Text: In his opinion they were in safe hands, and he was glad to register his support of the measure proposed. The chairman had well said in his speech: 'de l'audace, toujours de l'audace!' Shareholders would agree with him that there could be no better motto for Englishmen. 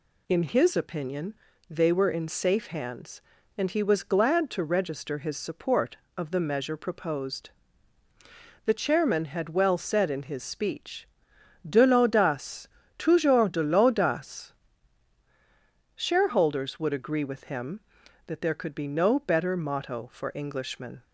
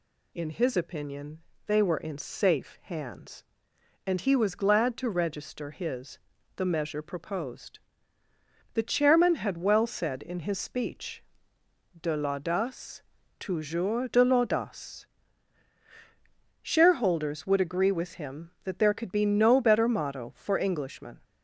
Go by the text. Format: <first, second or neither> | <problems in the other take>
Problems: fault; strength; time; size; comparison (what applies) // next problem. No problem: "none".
first | pauses between "opinion" and "they"; slight; at 1.4 s; 0.26 s long; slight in the first // skips "support of"; at 6.3 s